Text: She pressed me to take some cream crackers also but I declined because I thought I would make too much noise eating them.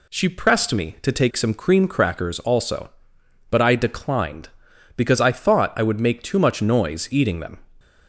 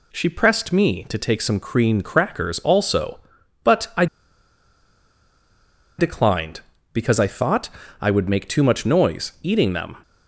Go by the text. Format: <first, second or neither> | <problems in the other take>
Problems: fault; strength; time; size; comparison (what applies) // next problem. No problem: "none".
first | pauses between "I" and "declined"; strong; at 4.0 s; 1.9 s long // pauses between "thought" and "I"; slight; at 7.6 s; 0.32 s long